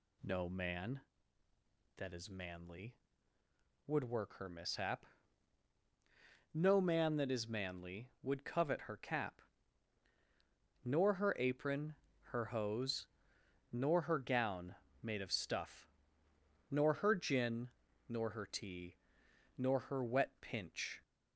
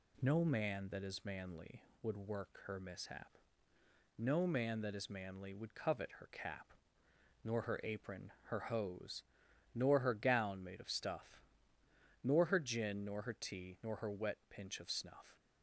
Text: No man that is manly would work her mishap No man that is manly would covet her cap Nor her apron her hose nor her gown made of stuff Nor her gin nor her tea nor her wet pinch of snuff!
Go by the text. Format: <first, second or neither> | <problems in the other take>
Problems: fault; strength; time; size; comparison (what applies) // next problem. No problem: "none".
second | pauses between "mishap" and "No"; strong; at 5.0 s; 1.4 s long; noticeable in the second // pauses between "cap" and "Nor"; strong; at 9.3 s; 1.4 s long; noticeable in the second // pauses between "apron" and "her"; slight; at 11.9 s; 0.30 s long // pauses between "hose" and "nor"; noticeable; at 13.0 s; 0.66 s long; noticeable in the second // pauses between "gown" and "made"; slight; at 14.7 s; 0.28 s long // pauses between "stuff" and "Nor"; noticeable; at 15.8 s; 0.82 s long; noticeable in the second // pauses between "gin" and "nor"; at 17.6 s; 0.38 s long // pauses between "tea" and "nor"; noticeable; at 18.9 s; 0.62 s long // stops before "of snuff"; at 21.0 s